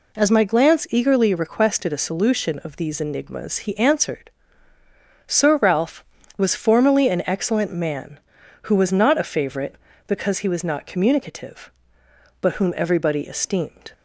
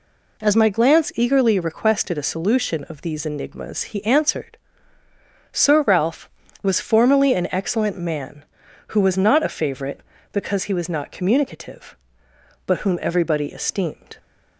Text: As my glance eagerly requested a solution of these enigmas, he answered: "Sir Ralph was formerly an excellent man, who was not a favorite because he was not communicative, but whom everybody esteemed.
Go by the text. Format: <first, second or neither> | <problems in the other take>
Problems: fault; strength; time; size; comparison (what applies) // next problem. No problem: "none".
neither | none